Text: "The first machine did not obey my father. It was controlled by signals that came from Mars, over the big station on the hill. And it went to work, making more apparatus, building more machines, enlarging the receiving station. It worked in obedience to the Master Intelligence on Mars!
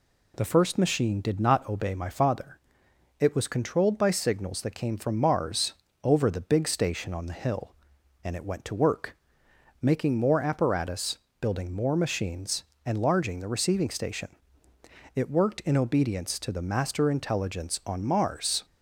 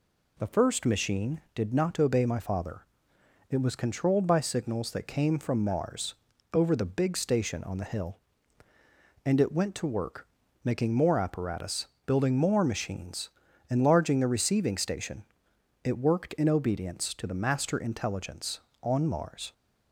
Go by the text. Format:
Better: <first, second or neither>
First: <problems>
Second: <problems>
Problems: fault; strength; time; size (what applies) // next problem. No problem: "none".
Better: neither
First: none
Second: none